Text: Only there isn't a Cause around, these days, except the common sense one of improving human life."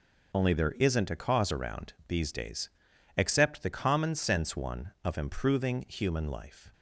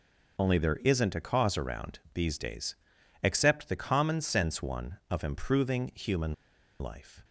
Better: first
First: none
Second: pauses between "human" and "life"; noticeable; at 6.3 s; 0.47 s long

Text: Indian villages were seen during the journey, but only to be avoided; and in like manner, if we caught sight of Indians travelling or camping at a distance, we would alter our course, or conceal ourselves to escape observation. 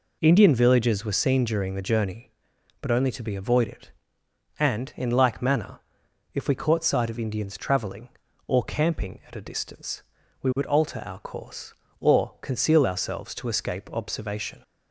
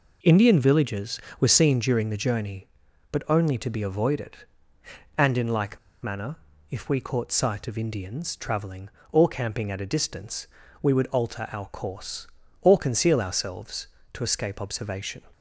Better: first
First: none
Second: pauses between "like" and "manner"; slight; at 5.7 s; 0.25 s long

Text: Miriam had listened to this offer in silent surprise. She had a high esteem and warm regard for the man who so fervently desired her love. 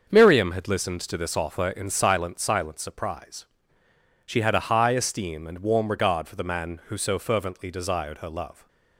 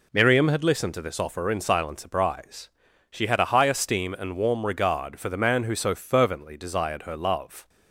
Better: second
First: starts louder than the rest; until 1.1 s; 6.5 dB // says "silent" twice; at 2.3 s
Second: none

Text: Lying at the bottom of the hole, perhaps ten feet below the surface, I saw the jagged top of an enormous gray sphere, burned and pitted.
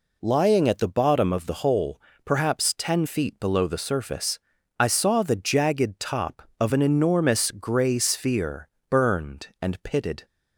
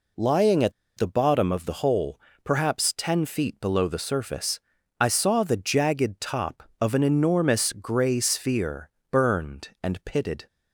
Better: first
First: none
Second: pauses between "at" and "the"; slight; at 0.7 s; 0.24 s long

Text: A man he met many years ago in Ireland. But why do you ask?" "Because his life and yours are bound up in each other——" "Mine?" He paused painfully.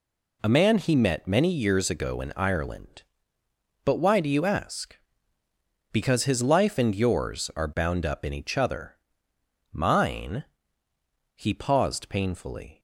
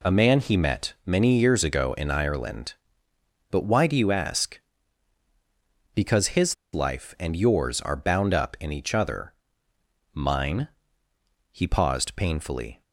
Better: first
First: none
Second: pauses between "his" and "life"; slight; at 6.5 s; 0.19 s long

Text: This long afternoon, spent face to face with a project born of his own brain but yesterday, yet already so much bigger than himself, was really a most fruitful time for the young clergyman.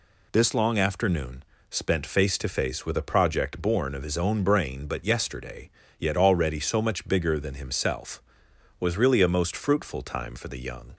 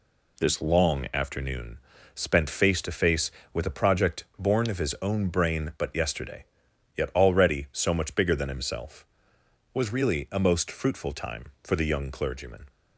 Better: second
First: stops before "clergyman"; at 10.9 s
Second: none

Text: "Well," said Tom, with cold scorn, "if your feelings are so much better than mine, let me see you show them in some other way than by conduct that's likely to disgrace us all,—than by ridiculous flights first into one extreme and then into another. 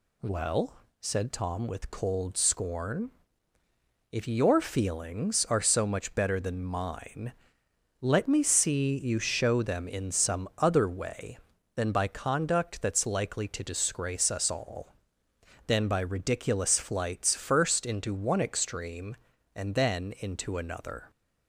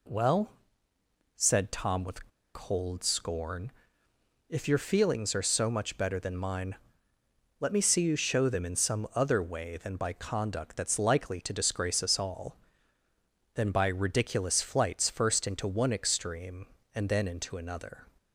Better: first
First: none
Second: pauses between "with" and "cold"; slight; at 2.2 s; 0.25 s long

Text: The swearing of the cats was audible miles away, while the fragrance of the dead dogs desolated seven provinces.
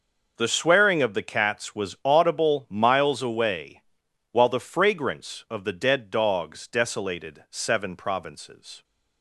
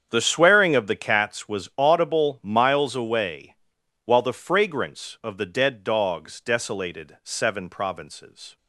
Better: first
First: none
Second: starts louder than the rest; strong; until 1.4 s; 8 dB

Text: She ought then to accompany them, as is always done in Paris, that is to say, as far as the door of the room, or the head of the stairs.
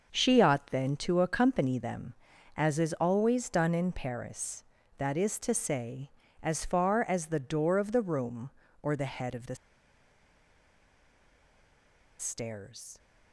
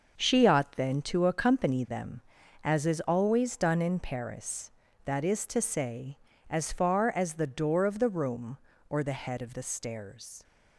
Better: second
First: starts louder than the rest; until 1.2 s; 6.5 dB // pauses between "the" and "stairs"; strong; at 9.5 s; 2.6 s long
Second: starts louder than the rest; until 1.3 s; 7 dB

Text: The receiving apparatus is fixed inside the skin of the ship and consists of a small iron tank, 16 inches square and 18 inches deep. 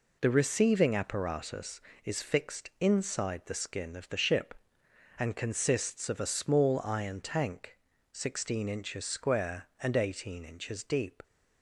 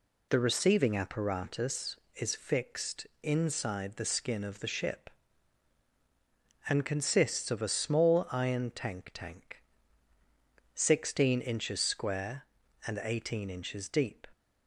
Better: first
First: none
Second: pauses between "fixed" and "inside"; slight; at 3.0 s; 0.16 s long // says "tank" twice; at 9.1 s

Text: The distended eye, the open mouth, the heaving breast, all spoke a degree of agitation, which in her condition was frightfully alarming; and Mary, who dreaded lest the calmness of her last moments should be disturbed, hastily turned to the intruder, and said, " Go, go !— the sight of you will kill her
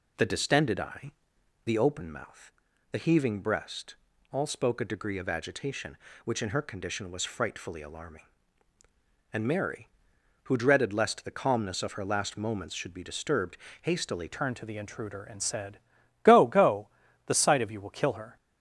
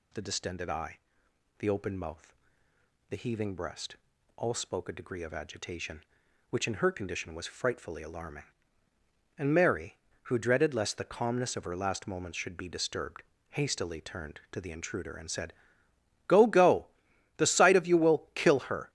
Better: second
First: changes voice at "turned"; from 14.3 s on; 4.0 s long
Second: none

